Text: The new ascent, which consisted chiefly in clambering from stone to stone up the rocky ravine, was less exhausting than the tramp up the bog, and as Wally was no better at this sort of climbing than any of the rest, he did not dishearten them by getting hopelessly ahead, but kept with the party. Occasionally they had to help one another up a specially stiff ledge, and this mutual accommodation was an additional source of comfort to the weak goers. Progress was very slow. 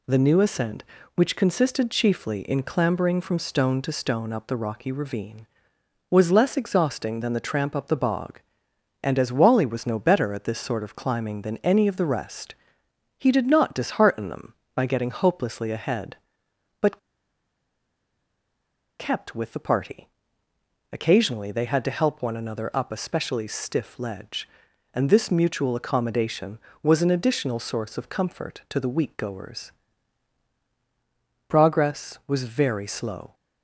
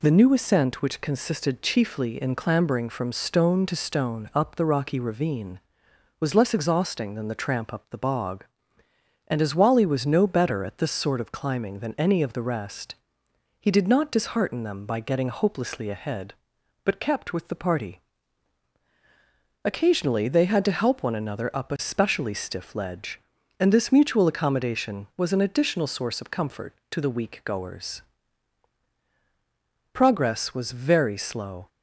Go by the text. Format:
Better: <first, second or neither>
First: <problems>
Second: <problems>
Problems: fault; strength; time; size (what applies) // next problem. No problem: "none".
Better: second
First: pauses between "but" and "kept"; strong; at 16.9 s; 2.0 s long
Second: none